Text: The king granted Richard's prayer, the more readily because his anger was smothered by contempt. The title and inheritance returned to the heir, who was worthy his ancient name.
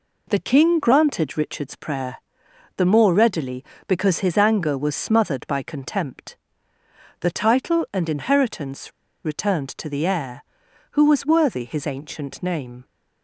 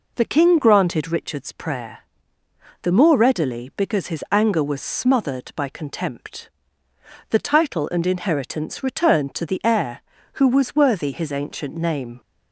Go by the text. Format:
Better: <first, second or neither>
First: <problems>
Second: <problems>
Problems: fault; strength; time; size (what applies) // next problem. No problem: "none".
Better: second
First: pauses between "inheritance" and "returned"; slight; at 8.9 s; 0.33 s long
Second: none